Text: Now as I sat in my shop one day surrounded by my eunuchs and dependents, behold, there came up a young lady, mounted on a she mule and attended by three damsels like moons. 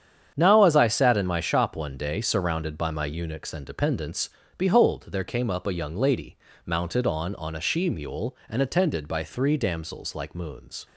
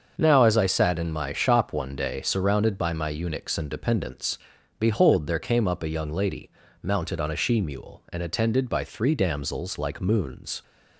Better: second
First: starts louder than the rest; strong; until 1.3 s; 8.5 dB // says "on" twice; at 7.3 s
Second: starts louder than the rest; until 1.1 s; 6.5 dB

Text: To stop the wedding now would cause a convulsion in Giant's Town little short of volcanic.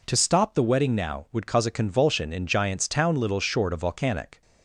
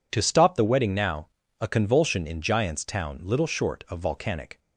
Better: first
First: none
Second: skips "would cause"; at 1.4 s

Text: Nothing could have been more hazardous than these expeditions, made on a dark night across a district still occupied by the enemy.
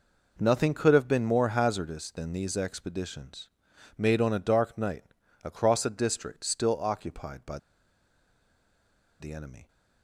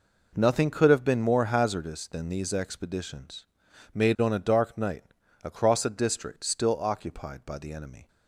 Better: second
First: pauses between "night" and "across"; at 5.0 s; 0.40 s long // pauses between "by" and "the"; strong; at 7.5 s; 1.6 s long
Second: pauses between "night" and "across"; at 5.0 s; 0.40 s long

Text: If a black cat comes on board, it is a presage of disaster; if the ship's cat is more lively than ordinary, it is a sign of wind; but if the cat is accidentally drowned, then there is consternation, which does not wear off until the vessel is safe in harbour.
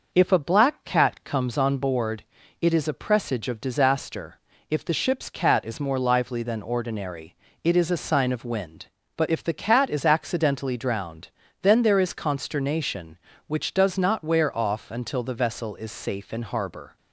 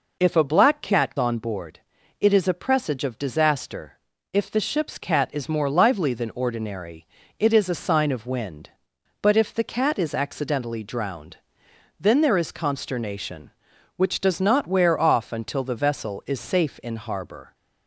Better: first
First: none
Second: skips "comes"; at 1.1 s

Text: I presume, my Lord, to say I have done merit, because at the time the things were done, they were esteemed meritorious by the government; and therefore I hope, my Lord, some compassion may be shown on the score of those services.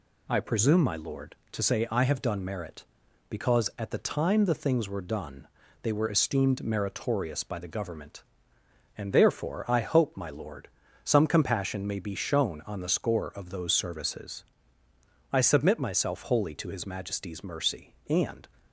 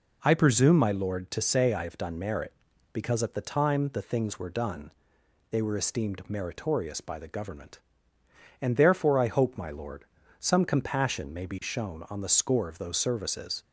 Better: second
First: goes on to say "I submit myself wholly to his Majesty's mercy and"; strong; from 15.2 s on; 3.1 s long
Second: none

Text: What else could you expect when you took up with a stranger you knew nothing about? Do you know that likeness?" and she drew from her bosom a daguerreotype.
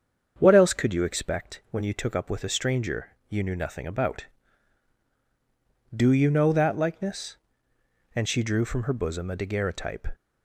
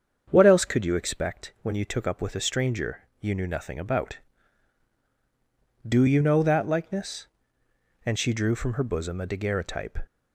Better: neither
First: starts louder than the rest; strong; until 1.3 s; 7.5 dB // pauses between "stranger" and "you"; slight; at 3.0 s; 0.18 s long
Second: starts louder than the rest; strong; until 1.3 s; 7.5 dB // pauses between "stranger" and "you"; slight; at 3.0 s; 0.18 s long

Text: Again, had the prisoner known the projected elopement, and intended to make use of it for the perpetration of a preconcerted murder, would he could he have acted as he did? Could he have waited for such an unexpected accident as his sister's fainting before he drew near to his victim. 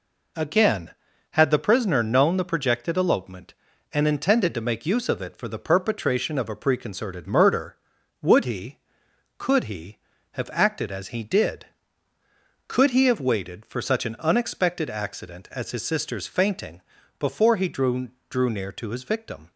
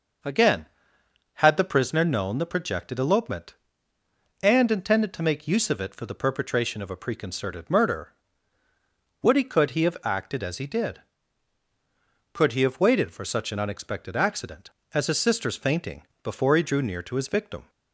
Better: second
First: pauses between "fainting" and "before"; slight; at 16.8 s; 0.36 s long // says "drew" twice; at 18.2 s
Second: pauses between "fainting" and "before"; slight; at 16.0 s; 0.20 s long

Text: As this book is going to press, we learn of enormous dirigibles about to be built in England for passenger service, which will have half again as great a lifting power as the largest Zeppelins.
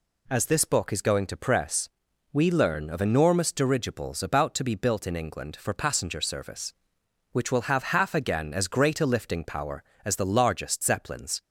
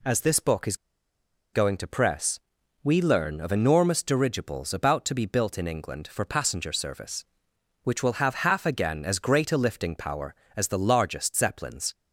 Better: first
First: none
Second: pauses between "is" and "going"; noticeable; at 0.7 s; 0.77 s long

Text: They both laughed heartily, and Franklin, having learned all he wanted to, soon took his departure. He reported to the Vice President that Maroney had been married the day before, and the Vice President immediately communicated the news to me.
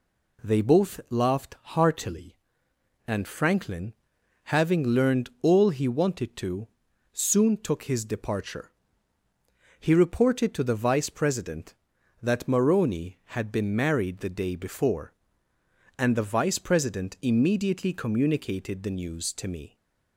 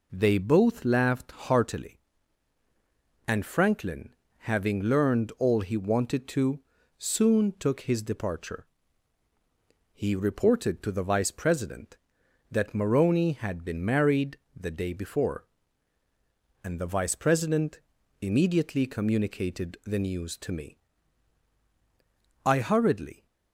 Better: first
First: none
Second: pauses between "married" and "the"; slight; at 14.3 s; 0.18 s long // pauses between "President" and "immediately"; at 17.7 s; 0.42 s long // goes on to say "I hurriedly"; noticeable; from 22.4 s on; 0.82 s long

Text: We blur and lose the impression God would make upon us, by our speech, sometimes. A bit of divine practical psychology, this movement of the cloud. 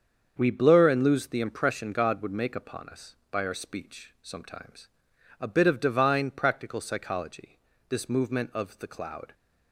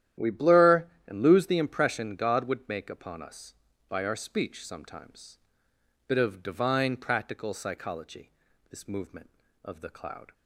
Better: first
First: starts louder than the rest; until 1.3 s; 7 dB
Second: starts louder than the rest; strong; until 1.3 s; 11.5 dB // skips "A"; at 5.7 s

